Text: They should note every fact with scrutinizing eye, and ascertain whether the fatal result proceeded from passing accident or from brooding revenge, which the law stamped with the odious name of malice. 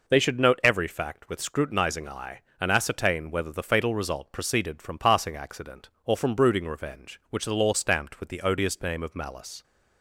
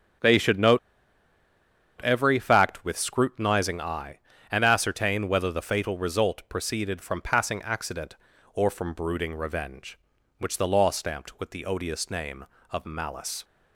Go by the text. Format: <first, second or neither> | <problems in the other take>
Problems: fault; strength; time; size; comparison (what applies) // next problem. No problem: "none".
first | starts louder than the rest; strong; until 2.4 s; 7.5 dB // pauses between "note" and "every"; at 0.7 s; 1.2 s long